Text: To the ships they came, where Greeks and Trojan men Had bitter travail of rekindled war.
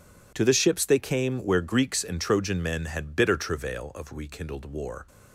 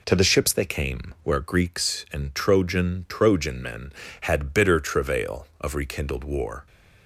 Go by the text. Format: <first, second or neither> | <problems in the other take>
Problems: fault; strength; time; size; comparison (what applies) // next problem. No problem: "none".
first | says "Trojan" twice; at 3.0 s